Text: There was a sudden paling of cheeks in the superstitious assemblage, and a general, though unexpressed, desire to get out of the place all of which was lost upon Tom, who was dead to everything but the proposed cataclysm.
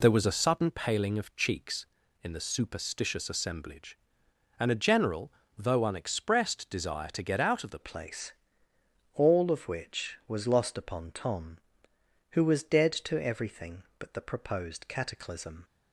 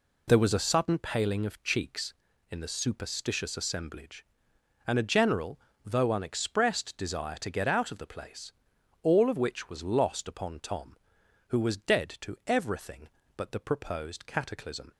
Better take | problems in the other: second | changes voice at "place"; from 7.8 s on; 7.8 s long // pauses between "place" and "all"; noticeable; at 8.3 s; 0.82 s long; noticeable in the second

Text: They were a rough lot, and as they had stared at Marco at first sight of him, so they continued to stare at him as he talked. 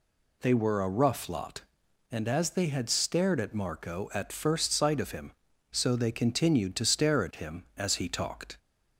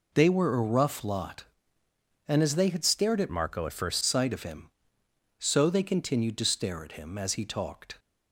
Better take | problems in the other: first | changes voice from "Marco" to "first"; from 3.2 to 4.0 s; 0.8 s long

